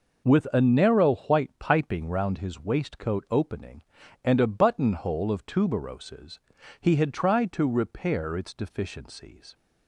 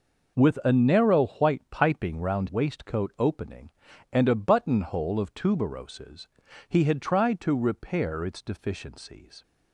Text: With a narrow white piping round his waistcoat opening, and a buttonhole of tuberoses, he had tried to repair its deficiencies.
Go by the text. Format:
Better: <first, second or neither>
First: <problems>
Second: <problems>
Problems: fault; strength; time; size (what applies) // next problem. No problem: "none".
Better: first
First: none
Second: skips "his"; at 2.4 s